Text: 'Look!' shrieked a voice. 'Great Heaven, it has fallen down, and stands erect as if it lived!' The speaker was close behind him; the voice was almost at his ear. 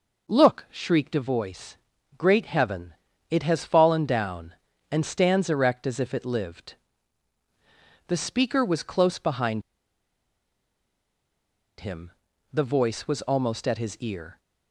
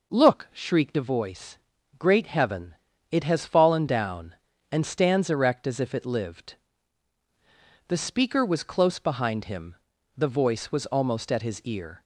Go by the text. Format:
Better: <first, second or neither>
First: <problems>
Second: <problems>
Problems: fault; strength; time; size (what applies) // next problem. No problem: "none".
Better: second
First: pauses between "behind" and "him"; strong; at 9.6 s; 2.1 s long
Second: none